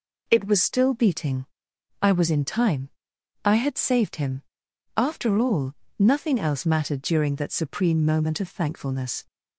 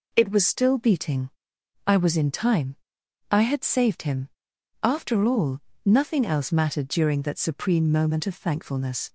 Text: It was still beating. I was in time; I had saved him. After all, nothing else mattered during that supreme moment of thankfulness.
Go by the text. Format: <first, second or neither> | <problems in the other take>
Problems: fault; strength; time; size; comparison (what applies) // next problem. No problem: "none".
neither | none